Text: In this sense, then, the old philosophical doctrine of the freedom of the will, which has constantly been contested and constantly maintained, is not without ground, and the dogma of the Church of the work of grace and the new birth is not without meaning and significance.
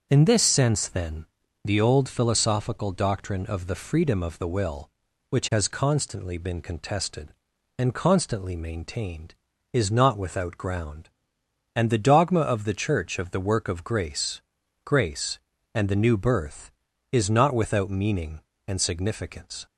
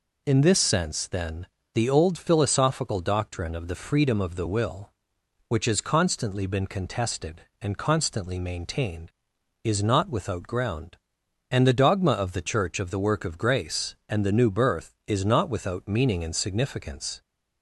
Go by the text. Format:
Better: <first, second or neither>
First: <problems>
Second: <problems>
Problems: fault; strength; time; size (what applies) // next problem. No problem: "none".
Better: second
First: starts louder than the rest; until 1.1 s; 6.5 dB // says "grace" twice; at 14.8 s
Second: none